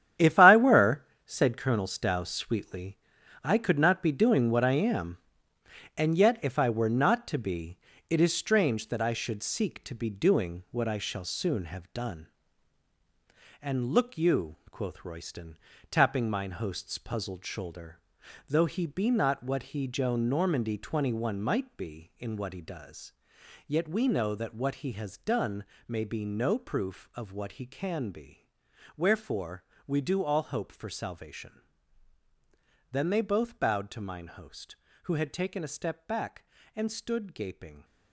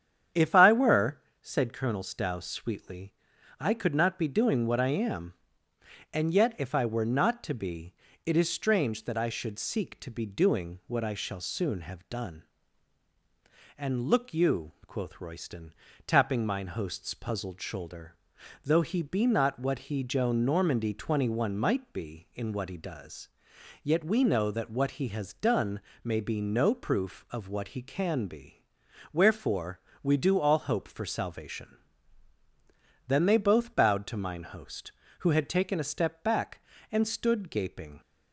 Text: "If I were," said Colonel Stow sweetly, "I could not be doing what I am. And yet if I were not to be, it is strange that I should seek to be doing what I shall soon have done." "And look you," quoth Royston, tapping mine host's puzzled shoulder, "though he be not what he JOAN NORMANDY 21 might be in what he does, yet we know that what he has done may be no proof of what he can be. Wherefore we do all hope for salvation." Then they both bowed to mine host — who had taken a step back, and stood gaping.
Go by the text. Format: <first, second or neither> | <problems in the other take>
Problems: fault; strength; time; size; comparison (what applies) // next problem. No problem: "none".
second | gets quieter; strong; throughout; 10.5 dB // starts louder than the rest; strong; until 1.4 s; 10 dB; strong in the second // pauses between "done" and "may"; slight; at 25.6 s; 0.24 s long; slight in the second // pauses between "Wherefore" and "we"; slight; at 29.6 s; 0.22 s long; slight in the second